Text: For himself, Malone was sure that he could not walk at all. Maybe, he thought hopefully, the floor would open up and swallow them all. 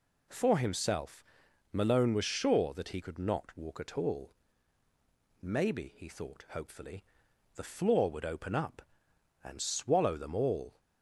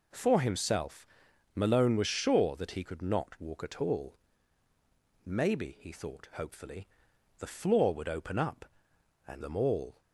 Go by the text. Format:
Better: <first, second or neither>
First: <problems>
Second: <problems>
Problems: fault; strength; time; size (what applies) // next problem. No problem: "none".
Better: first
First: none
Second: skips "swallow"; at 9.4 s